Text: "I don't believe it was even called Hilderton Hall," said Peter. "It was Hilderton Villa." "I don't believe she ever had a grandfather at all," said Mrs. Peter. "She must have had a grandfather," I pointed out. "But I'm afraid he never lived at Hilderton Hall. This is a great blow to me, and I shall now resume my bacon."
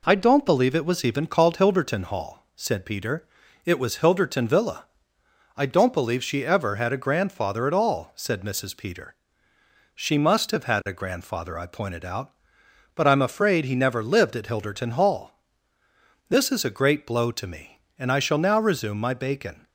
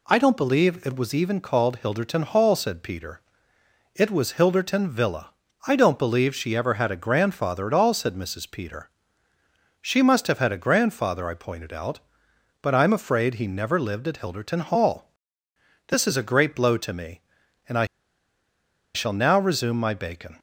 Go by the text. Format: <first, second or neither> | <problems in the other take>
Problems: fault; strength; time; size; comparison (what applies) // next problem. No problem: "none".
first | pauses between "I" and "shall"; at 17.8 s; 1.0 s long